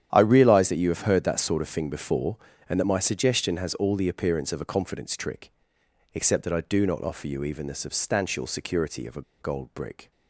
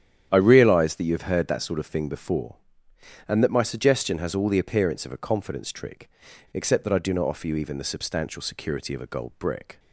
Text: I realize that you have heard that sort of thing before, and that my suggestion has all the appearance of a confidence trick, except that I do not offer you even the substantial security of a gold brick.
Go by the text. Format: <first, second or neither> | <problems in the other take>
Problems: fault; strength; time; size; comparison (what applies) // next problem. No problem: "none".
second | starts louder than the rest; strong; until 1.1 s; 10 dB; strong in the second // pauses between "a" and "gold"; slight; at 9.2 s; 0.18 s long